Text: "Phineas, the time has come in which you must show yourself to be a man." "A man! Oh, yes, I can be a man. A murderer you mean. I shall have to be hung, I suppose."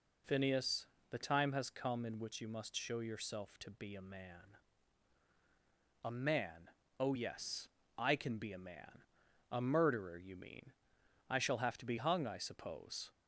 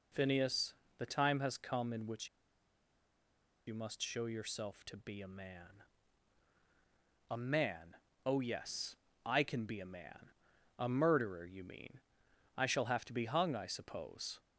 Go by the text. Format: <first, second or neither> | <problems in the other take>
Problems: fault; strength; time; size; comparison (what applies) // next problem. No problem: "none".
first | pauses between "which" and "you"; strong; at 2.2 s; 1.3 s long